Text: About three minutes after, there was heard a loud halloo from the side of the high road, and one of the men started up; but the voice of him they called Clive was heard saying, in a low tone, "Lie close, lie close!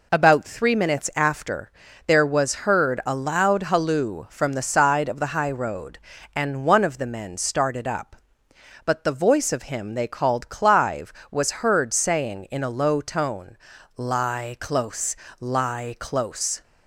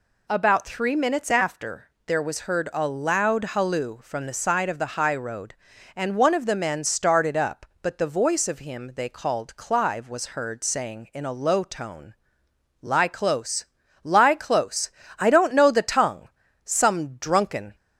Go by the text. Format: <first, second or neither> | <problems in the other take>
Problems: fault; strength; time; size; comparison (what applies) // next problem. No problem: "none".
first | goes on to say "I don't know the tongue some drunken"; strong; from 15.1 s on; 2.5 s long